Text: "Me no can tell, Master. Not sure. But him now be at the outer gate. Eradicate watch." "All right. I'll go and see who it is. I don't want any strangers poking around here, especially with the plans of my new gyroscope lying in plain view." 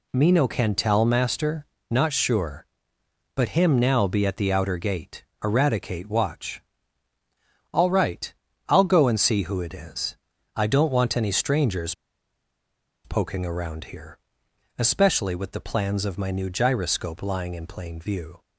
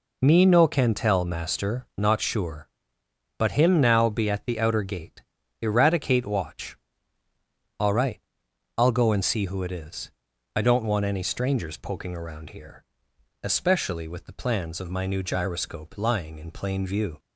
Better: second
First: pauses between "strangers" and "poking"; at 11.9 s; 1.1 s long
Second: none

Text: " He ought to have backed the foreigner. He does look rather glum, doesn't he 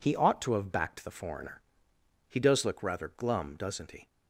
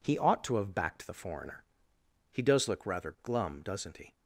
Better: neither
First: none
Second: none

